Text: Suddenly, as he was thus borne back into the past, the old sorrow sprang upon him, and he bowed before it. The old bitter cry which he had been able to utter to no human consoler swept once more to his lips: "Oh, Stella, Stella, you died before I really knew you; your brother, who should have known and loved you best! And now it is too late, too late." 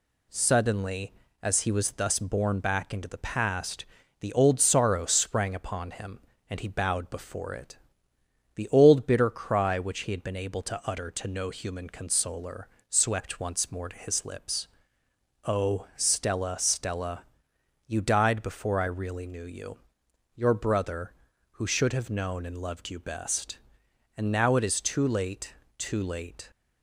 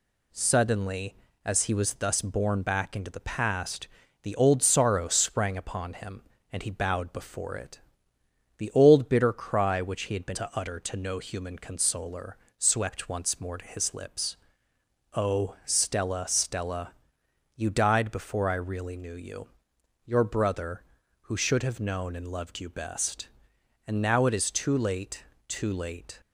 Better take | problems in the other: first | skips "able"; at 10.3 s // pauses between "consoler" and "swept"; slight; at 12.3 s; 0.22 s long; slight in the first

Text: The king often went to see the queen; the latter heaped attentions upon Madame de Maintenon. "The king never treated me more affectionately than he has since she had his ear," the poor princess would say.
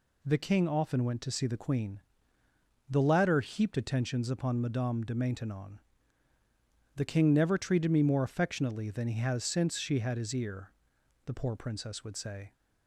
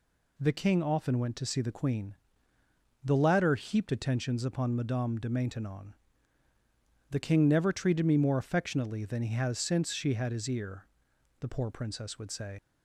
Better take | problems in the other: first | leaves "say" unfinished; at 12.5 s; 75 ms

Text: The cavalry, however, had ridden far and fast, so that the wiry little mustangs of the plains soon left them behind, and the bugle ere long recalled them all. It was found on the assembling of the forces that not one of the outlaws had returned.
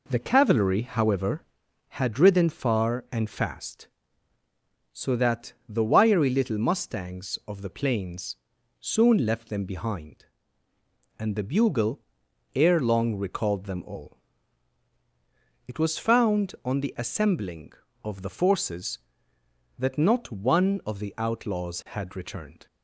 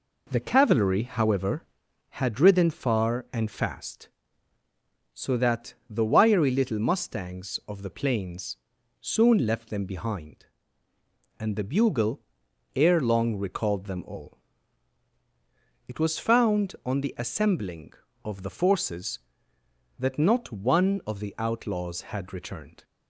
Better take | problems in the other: neither | pauses between "that" and "the"; slight; the same in both // pauses between "plains" and "soon"; the same in both // pauses between "bugle" and "ere"; noticeable; the same in both

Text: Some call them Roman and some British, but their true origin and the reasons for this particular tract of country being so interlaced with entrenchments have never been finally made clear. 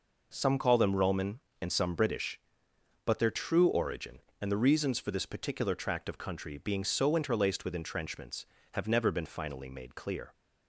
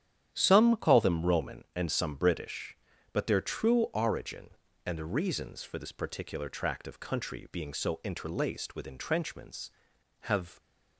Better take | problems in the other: first | starts louder than the rest; strong; until 1.3 s; 10 dB // stops before "never been finally made clear"; at 10.5 s

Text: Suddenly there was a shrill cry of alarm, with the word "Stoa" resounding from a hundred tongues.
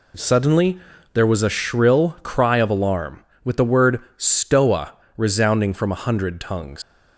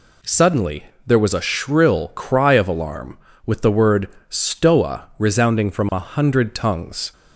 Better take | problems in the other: second | pauses between "Suddenly" and "there"; slight; at 0.7 s; 0.33 s long; slight in the second // pauses between "word" and "Stoa"; slight; at 3.9 s; 0.18 s long; slight in the second // pauses between "Stoa" and "resounding"; slight; at 4.9 s; 0.24 s long // leaves "tongues" unfinished; at 6.8 s; 110 ms

